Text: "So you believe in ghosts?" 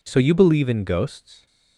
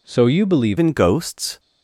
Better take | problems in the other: first | changes voice at "in"; from 0.7 s on; 0.8 s long

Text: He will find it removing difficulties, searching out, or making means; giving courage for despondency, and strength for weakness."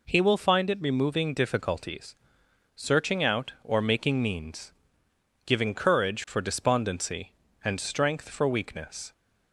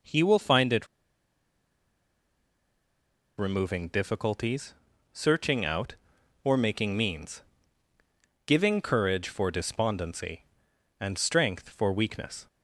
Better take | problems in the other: first | pauses between "it" and "removing"; strong; at 0.8 s; 2.5 s long

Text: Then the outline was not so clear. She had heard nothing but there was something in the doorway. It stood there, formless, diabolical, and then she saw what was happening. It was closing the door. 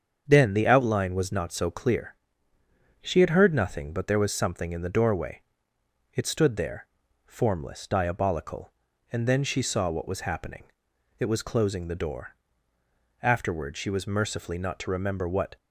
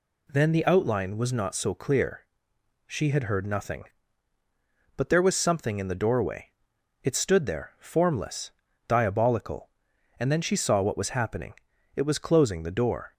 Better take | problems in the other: second | starts louder than the rest; strong; until 1.2 s; 7 dB // goes on to say "Afterward she was mercifully not to remember what"; strong; from 13.2 s on; 2.3 s long

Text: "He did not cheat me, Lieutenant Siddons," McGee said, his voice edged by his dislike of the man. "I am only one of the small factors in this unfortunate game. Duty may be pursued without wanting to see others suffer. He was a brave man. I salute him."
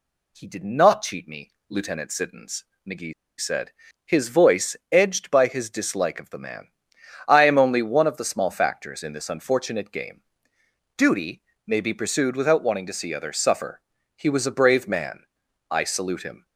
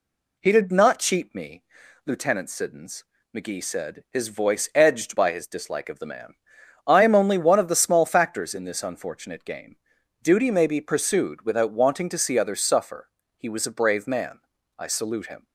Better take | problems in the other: second | pauses between "McGee" and "said"; slight; at 3.1 s; 0.27 s long // pauses between "voice" and "edged"; slight; at 4.7 s; 0.16 s long // pauses between "Duty" and "may"; slight; at 11.4 s; 0.26 s long

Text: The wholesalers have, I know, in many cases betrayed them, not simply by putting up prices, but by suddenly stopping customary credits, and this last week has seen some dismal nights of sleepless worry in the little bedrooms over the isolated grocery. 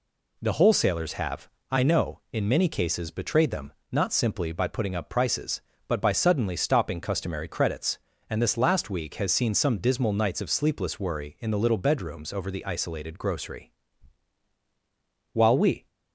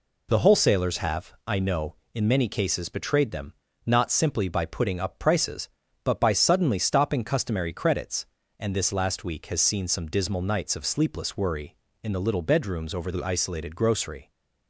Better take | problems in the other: second | goes on to say "While we"; from 15.3 s on; 0.54 s long

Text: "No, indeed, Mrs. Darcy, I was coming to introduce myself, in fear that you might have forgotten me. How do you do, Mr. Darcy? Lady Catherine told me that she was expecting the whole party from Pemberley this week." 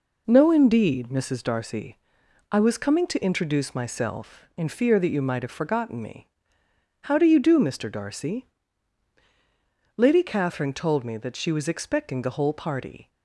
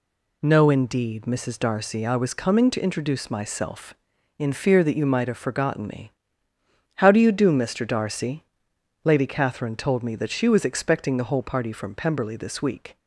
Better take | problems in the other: second | stops before "from Pemberley this week"; at 13.1 s

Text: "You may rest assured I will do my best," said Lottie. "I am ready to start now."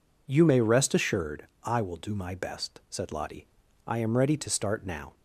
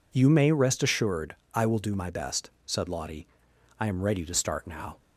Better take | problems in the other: neither | pauses between "assured" and "I"; slight; the same in both

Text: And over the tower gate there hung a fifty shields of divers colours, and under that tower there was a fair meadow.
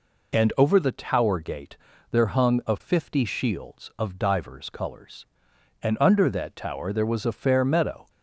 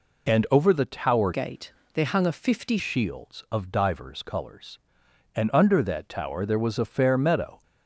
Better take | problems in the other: first | changes voice from "gate" to "fifty"; from 1.3 to 2.7 s; 1.4 s long // pauses between "gate" and "there"; slight; at 1.7 s; 0.24 s long; slight in the first

